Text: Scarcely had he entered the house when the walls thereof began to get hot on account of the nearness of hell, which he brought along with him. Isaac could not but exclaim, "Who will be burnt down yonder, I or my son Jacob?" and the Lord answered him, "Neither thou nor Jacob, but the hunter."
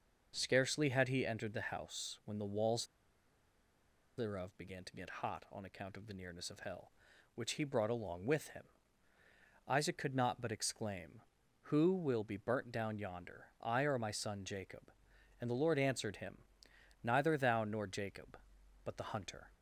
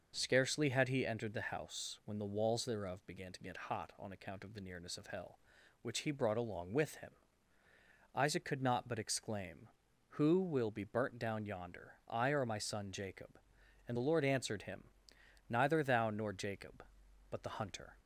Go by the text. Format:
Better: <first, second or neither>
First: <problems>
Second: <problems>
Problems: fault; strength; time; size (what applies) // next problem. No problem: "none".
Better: second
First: starts louder than the rest; noticeable; until 1.3 s; 6 dB // pauses between "walls" and "thereof"; strong; at 2.8 s; 1.3 s long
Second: starts louder than the rest; noticeable; until 1.1 s; 6 dB